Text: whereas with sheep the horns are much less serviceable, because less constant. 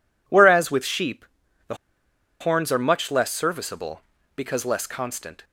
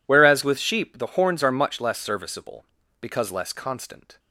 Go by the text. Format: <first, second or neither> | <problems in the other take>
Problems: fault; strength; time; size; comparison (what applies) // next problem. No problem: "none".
second | pauses between "sheep" and "the"; at 1.2 s; 0.42 s long // pauses between "the" and "horns"; noticeable; at 1.7 s; 0.66 s long